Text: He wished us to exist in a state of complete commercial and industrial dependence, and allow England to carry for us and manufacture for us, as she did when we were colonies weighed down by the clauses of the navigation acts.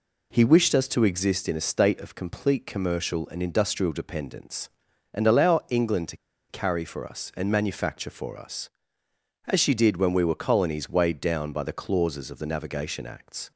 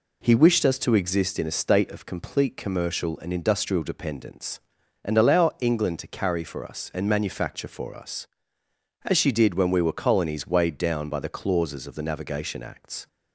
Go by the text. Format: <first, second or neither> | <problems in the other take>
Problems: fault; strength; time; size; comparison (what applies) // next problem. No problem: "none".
second | pauses between "to" and "carry"; slight; at 6.1 s; 0.33 s long